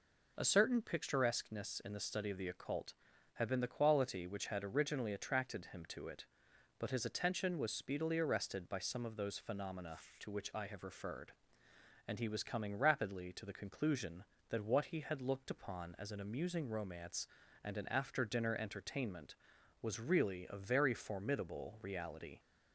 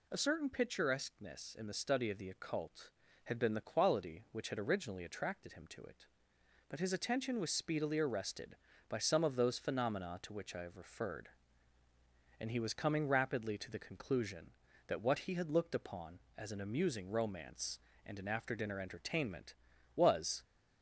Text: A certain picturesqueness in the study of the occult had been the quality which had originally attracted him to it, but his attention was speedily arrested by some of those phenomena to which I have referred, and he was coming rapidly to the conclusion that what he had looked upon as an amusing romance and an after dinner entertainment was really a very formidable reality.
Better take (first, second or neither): first